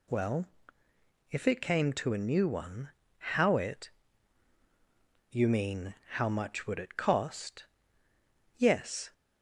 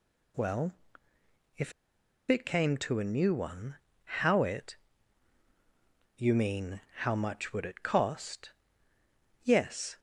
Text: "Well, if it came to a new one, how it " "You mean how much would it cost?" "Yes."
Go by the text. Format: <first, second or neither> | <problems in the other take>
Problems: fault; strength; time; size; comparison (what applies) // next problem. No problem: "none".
first | pauses between "if" and "it"; noticeable; at 1.7 s; 0.56 s long